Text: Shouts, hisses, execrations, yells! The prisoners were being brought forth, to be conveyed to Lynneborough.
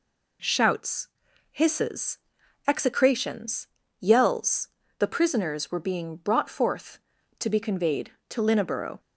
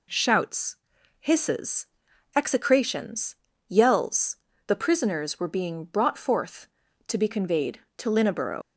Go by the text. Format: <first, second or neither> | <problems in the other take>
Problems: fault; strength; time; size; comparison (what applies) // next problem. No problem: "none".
first | leaves "Lynneborough" unfinished; at 8.6 s; 65 ms